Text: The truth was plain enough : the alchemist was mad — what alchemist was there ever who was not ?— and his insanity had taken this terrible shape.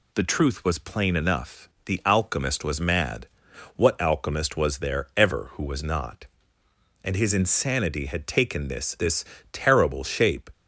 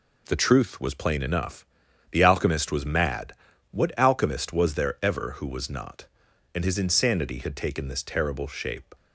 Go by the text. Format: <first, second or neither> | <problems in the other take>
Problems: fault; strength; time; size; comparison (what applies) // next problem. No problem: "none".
second | says "this" twice; at 8.9 s